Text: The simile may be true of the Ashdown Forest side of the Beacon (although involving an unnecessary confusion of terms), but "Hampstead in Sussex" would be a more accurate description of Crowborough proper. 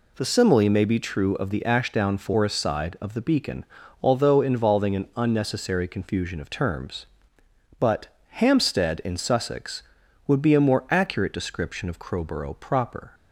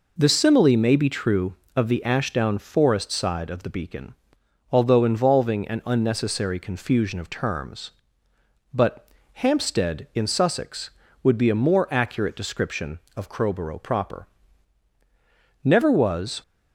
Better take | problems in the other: first | pauses between "but" and "Hampstead"; slight; at 9.0 s; 0.26 s long; slight in the first // goes on to say "Never was"; noticeable; from 15.6 s on; 0.78 s long

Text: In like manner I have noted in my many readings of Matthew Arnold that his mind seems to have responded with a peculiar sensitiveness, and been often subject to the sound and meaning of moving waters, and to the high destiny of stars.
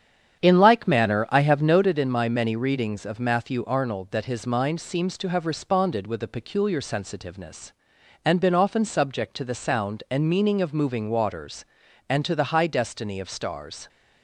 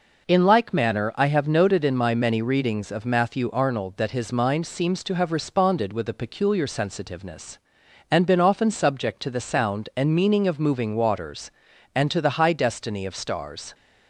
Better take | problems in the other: second | starts louder than the rest; strong; until 1.9 s; 9 dB

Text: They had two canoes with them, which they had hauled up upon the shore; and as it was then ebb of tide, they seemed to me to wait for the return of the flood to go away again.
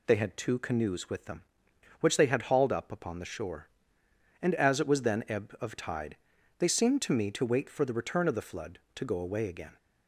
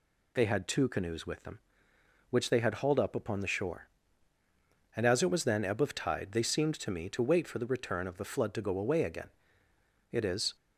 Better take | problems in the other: first | goes on to say "It is"; slight; from 10.1 s on; 0.44 s long

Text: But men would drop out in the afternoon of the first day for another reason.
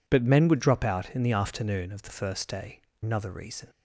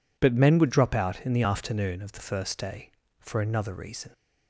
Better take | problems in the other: second | skips "for"; at 2.9 s

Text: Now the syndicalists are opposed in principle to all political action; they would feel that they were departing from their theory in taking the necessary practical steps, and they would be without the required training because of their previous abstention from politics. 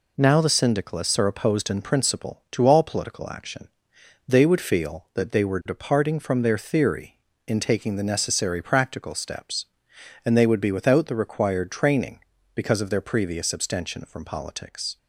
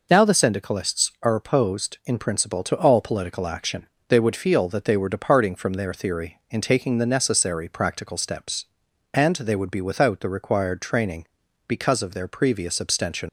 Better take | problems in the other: first | stops before "from politics"; at 13.2 s

